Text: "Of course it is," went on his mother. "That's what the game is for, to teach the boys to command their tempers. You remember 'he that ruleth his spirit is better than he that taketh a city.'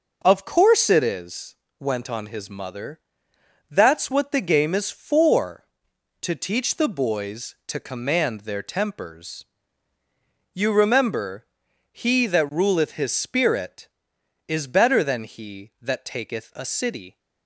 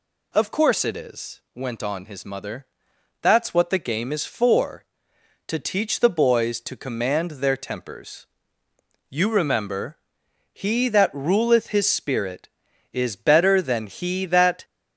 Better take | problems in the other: first | pauses between "remember" and "he"; noticeable; at 9.9 s; 0.52 s long; also in the first // stops before "taketh a city"; at 14.6 s

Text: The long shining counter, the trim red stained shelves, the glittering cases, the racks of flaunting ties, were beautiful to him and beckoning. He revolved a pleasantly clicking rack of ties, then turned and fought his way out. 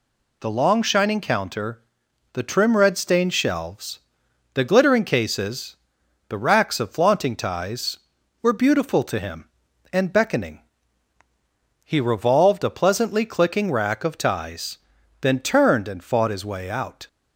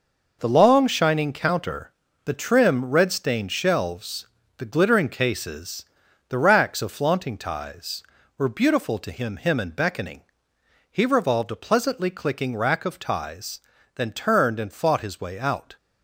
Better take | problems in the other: first | says "him" twice; at 9.3 s

